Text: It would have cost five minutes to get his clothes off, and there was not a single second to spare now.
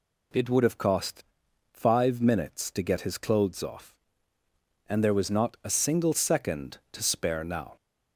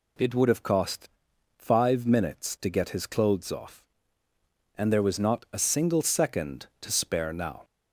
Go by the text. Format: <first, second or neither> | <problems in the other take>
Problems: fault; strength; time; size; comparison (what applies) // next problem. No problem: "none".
neither | pauses between "cost" and "five"; noticeable; the same in both